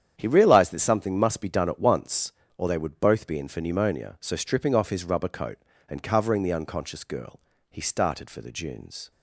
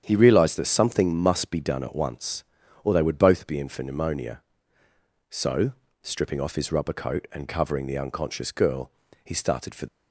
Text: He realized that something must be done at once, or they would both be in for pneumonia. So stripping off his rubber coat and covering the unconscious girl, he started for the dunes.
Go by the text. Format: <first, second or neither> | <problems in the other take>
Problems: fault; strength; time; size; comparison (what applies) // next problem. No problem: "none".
first | starts louder than the rest; strong; until 1.0 s; 8.5 dB; strong in the first // pauses between "So" and "stripping"; slight; at 5.7 s; 0.30 s long // stops before "the dunes"; at 9.8 s